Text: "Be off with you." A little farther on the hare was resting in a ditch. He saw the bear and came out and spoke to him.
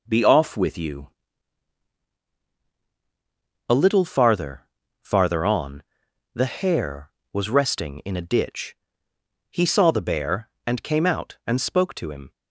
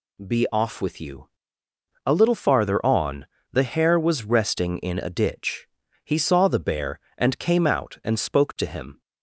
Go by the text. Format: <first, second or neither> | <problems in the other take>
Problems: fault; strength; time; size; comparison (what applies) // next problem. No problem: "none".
second | says "farther" twice; at 4.9 s // pauses between "on" and "the"; noticeable; at 5.8 s; 0.52 s long; slight in the second